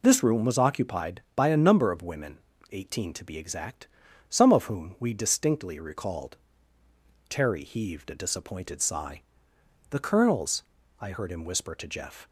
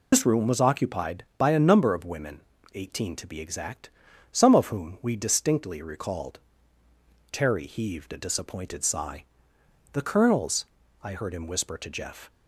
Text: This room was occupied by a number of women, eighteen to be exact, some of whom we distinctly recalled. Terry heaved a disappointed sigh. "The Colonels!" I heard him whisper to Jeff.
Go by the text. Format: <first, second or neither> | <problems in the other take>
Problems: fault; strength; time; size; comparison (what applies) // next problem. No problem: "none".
first | loses the start of "This"; at 0.1 s; 85 ms